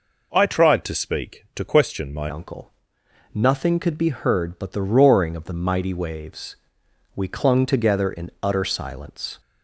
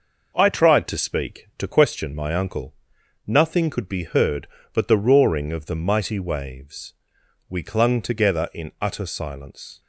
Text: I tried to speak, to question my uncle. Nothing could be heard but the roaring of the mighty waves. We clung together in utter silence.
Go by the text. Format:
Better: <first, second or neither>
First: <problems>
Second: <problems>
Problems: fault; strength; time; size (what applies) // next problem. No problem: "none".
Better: second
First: changes voice at "uncle"; from 2.2 s on; 7.1 s long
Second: none